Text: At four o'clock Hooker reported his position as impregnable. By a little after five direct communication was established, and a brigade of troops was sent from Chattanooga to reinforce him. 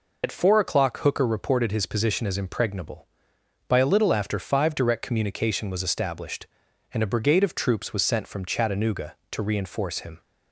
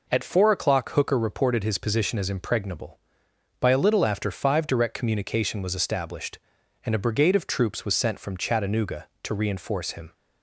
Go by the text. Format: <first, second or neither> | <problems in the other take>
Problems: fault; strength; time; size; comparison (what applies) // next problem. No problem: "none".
second | loses the start of "At"; at 0.2 s; 70 ms